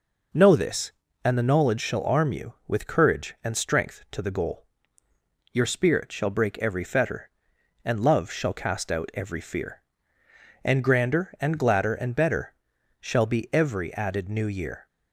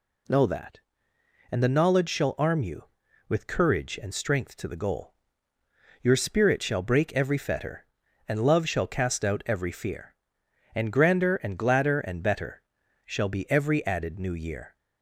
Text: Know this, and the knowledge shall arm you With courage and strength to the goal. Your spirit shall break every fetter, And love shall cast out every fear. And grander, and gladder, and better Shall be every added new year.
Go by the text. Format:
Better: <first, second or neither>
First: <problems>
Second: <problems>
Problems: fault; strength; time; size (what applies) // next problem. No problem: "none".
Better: first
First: pauses between "better" and "Shall"; noticeable; at 12.5 s; 0.46 s long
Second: says "that" for "this"; at 0.4 s // pauses between "better" and "Shall"; at 12.6 s; 0.44 s long